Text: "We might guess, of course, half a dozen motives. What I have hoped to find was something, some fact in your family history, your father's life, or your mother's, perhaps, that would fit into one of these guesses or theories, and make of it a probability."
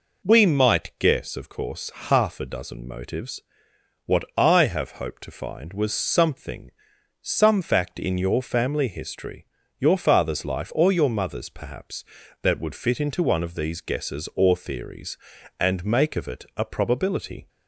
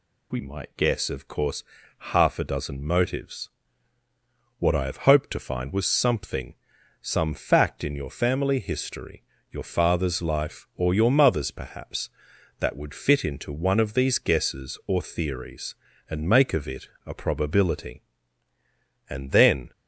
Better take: first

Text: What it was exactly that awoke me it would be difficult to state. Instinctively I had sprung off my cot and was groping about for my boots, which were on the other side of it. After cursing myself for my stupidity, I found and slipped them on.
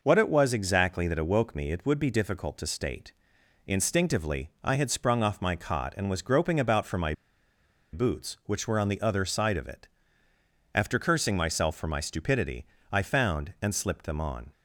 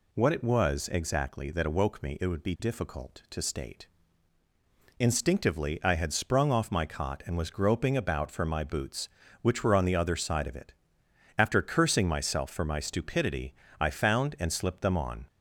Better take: second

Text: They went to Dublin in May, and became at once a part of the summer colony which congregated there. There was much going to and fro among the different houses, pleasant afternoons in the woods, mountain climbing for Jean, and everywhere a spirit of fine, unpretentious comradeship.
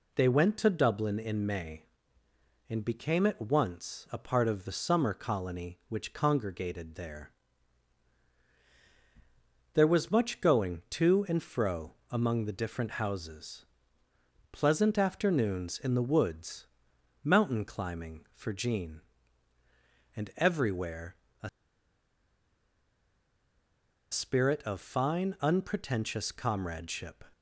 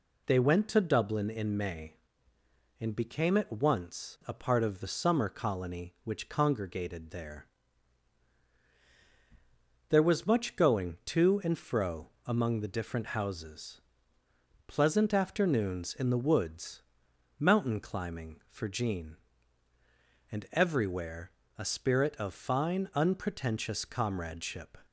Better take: second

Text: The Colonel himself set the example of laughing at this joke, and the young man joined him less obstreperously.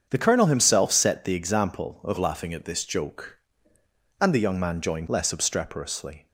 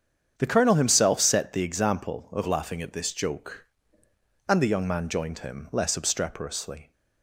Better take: second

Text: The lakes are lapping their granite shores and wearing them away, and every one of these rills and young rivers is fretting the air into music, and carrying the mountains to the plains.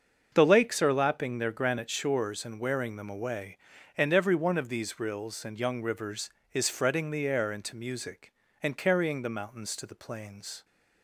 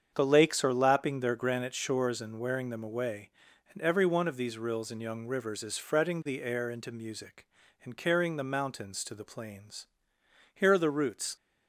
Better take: first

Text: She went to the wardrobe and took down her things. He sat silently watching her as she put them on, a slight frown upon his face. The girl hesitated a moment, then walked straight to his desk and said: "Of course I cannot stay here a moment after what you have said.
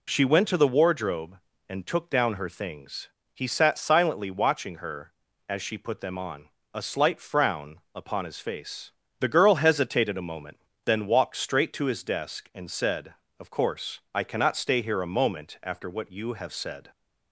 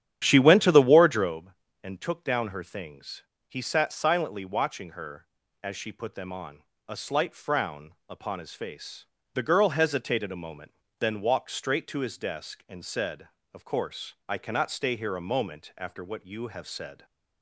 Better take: first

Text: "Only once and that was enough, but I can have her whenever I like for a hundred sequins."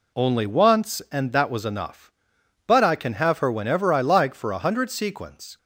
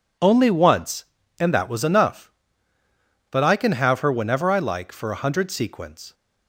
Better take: neither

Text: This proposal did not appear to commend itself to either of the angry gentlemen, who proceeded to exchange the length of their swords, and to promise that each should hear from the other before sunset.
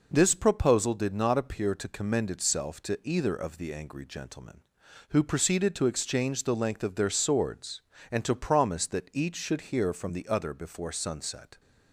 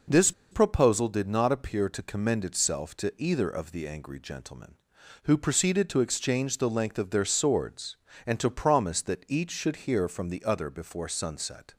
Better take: first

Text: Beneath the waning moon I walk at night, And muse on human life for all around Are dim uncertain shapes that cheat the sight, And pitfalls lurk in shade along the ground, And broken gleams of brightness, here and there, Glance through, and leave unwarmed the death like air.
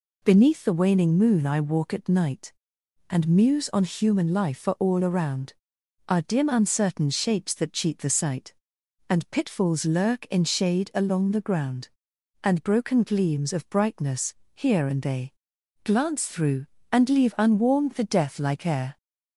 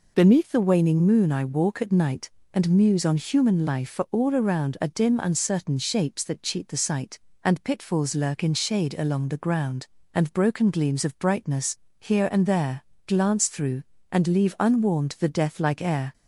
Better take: second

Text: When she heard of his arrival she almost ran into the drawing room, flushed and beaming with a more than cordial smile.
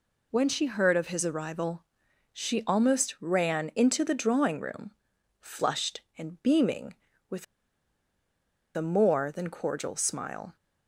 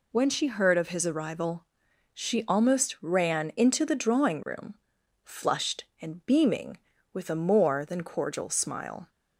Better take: second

